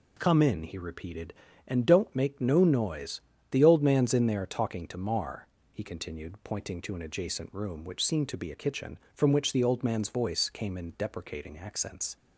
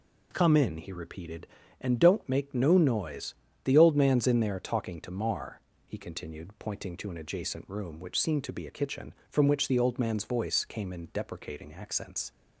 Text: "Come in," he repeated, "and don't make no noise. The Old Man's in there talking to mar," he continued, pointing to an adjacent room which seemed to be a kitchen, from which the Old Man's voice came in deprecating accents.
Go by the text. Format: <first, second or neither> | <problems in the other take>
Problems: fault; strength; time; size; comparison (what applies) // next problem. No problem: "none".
neither | none